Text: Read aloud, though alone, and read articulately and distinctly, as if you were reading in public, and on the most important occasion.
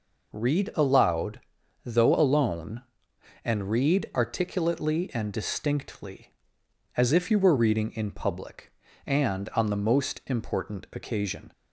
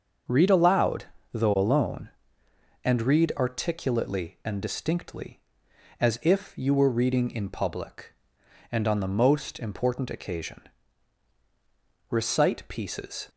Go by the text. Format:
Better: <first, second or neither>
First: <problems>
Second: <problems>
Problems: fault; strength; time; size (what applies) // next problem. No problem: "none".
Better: first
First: none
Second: starts louder than the rest; until 1.6 s; 6.5 dB // goes on to say "Recite pieces"; noticeable; from 12.0 s on; 1.2 s long